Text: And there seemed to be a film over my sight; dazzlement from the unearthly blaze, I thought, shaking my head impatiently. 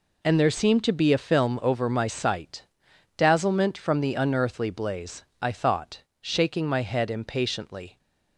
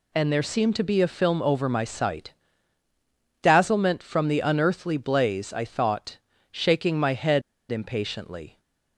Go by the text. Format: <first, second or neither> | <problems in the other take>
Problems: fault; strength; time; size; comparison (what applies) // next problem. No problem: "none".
first | pauses between "head" and "impatiently"; slight; at 7.4 s; 0.29 s long